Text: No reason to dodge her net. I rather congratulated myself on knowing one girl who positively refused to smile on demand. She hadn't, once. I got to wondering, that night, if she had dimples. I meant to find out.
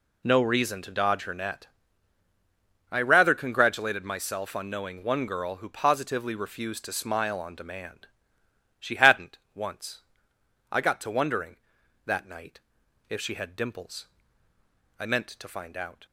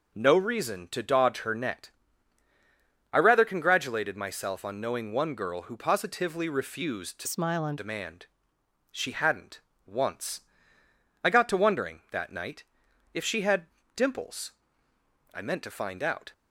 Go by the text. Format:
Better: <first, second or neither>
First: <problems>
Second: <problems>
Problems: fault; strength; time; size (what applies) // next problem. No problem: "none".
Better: first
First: none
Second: changes voice from "smile" to "on"; from 7.2 to 7.7 s; 0.5 s long // pauses between "had" and "dimples"; slight; at 13.6 s; 0.30 s long